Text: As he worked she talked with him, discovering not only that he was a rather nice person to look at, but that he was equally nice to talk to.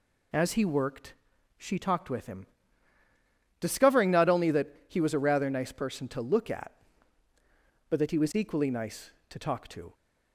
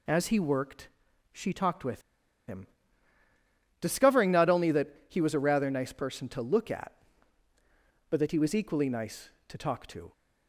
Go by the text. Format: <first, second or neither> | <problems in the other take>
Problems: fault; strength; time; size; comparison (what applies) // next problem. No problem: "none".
first | pauses between "worked" and "she"; at 0.8 s; 0.44 s long; also in the first // pauses between "with" and "him"; noticeable; at 1.9 s; 0.47 s long // pauses between "that" and "he"; slight; at 4.8 s; 0.22 s long; slight in the first